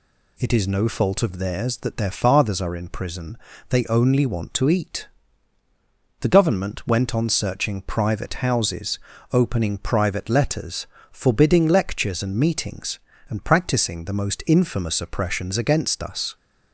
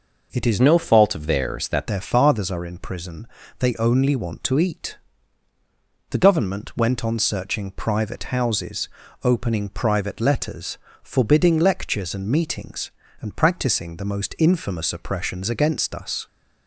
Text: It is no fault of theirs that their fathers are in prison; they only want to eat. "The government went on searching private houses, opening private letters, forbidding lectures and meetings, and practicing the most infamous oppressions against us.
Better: first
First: none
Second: changes voice from "no" to "that"; from 0.6 to 1.8 s; 1.2 s long

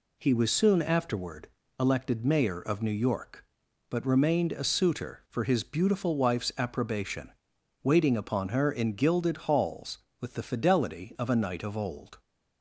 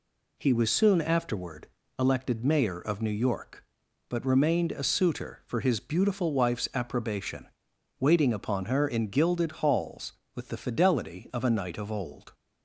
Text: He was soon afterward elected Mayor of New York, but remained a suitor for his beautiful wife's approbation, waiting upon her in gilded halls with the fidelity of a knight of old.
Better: neither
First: pauses between "afterward" and "elected"; slight; at 1.4 s; 0.30 s long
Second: pauses between "afterward" and "elected"; slight; at 1.6 s; 0.30 s long

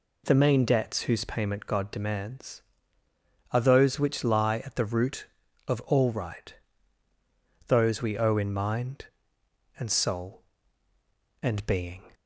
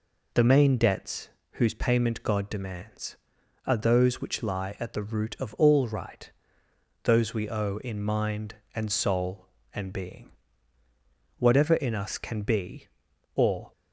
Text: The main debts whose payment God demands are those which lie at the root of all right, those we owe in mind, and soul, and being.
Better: first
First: none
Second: pauses between "debts" and "whose"; slight; at 1.2 s; 0.26 s long // goes on to say "Whatever in us can be or"; strong; from 11.3 s on; 2.3 s long

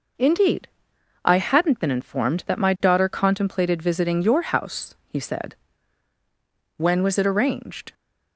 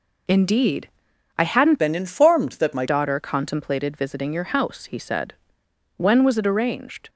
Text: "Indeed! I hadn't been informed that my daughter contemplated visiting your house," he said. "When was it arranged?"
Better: first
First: none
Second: changes voice from "been" to "my"; from 1.7 to 2.8 s; 1.1 s long

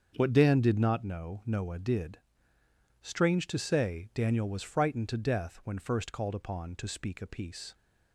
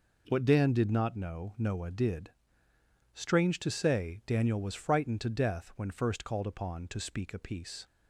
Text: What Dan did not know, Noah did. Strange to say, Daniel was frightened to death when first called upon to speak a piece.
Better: second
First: starts louder than the rest; until 1.1 s; 7 dB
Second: none

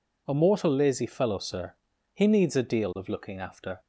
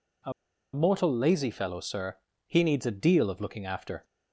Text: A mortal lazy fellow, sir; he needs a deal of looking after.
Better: first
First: none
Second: pauses between "A" and "mortal"; at 0.3 s; 0.42 s long

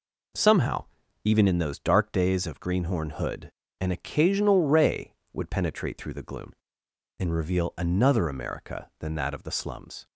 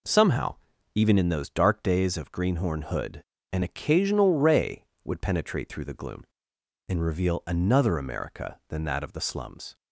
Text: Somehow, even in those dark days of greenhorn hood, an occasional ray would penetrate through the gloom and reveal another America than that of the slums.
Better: neither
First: none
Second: none

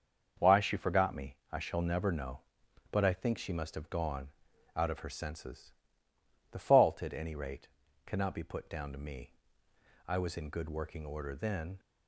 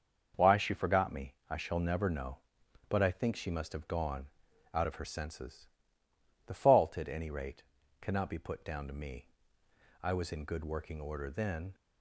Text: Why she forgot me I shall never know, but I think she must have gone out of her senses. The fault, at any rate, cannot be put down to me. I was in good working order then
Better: neither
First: starts louder than the rest; until 1.5 s; 6 dB // pauses between "me" and "I"; slight; at 1.3 s; 0.16 s long // pauses between "gone" and "out"; noticeable; at 4.2 s; 0.48 s long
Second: starts louder than the rest; until 1.5 s; 6 dB // pauses between "me" and "I"; slight; at 1.3 s; 0.16 s long // pauses between "gone" and "out"; noticeable; at 4.2 s; 0.48 s long

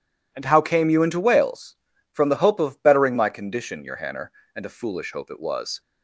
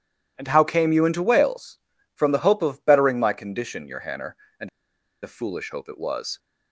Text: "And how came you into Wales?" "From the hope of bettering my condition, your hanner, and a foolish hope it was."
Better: first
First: none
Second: pauses between "and" and "a"; noticeable; at 4.6 s; 0.53 s long

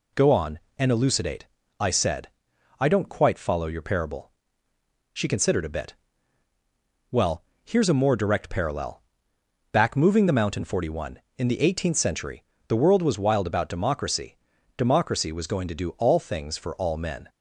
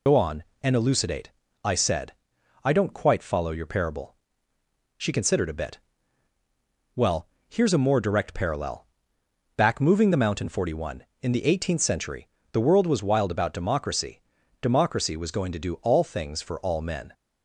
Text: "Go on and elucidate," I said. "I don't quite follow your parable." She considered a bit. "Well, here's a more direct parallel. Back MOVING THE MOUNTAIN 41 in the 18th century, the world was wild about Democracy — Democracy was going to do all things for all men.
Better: first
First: none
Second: loses the start of "Go"; at 0.0 s; 70 ms

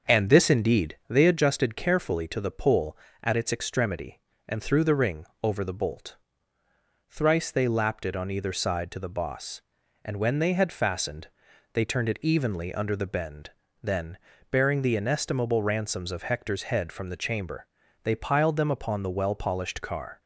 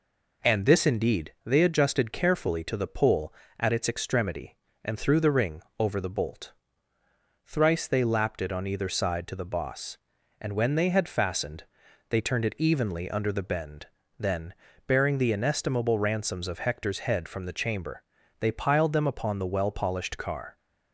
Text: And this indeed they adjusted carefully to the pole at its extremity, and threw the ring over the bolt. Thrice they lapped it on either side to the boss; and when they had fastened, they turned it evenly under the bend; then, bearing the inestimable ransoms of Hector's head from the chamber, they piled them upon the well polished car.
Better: second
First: starts louder than the rest; until 1.5 s; 6.5 dB // pauses between "ring" and "over"; slight; at 5.2 s; 0.16 s long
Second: pauses between "ring" and "over"; slight; at 5.6 s; 0.16 s long

